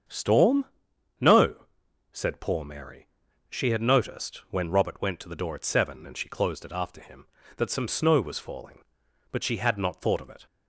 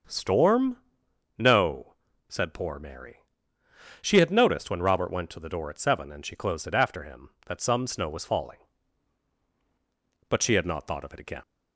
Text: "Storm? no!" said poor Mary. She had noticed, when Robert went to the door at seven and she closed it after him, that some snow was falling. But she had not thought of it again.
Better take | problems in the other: second | starts louder than the rest; strong; until 1.6 s; 7.5 dB; also in the second // stops before "again"; at 10.4 s

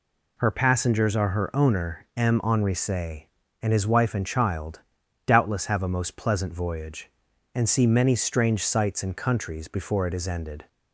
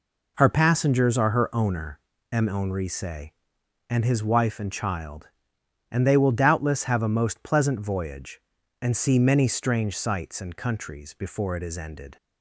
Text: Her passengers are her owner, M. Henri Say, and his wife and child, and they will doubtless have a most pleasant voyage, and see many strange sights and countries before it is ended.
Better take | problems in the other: second | skips "and they will"; at 5.0 s

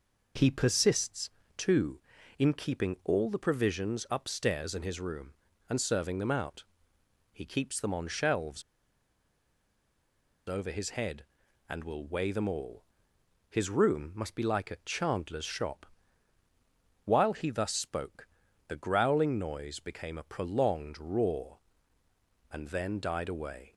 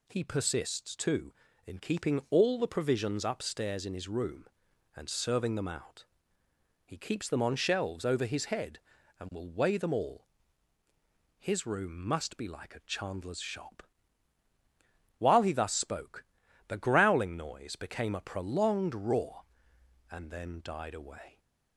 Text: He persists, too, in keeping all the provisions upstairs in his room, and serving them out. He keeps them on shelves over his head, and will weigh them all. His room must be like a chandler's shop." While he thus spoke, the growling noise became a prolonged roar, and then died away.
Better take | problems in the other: second | pauses between "shelves" and "over"; strong; at 8.6 s; 1.8 s long

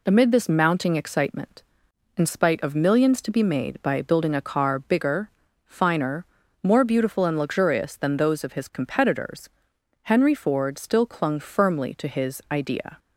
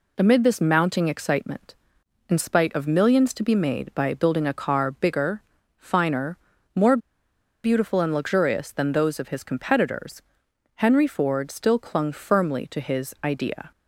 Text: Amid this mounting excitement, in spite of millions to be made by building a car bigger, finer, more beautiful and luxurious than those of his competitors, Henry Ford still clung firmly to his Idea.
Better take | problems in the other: first | pauses between "more" and "beautiful"; noticeable; at 6.9 s; 0.66 s long

